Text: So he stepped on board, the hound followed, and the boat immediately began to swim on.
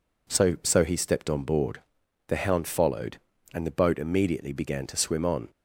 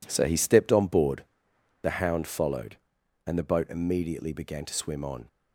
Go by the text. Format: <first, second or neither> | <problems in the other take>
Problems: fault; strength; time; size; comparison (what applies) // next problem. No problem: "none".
second | says "So" twice; at 0.6 s